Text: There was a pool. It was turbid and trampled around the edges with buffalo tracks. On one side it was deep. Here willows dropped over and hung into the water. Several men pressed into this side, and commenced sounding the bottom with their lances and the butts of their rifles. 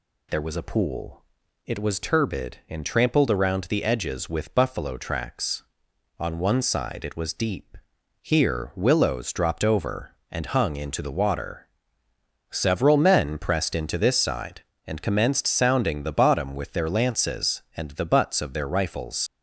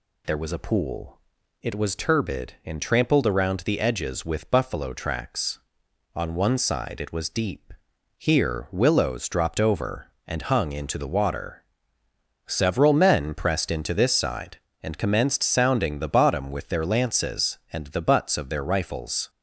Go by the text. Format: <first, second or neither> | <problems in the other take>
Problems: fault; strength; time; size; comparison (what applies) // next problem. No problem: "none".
second | leaves "rifles" unfinished; at 19.2 s; 70 ms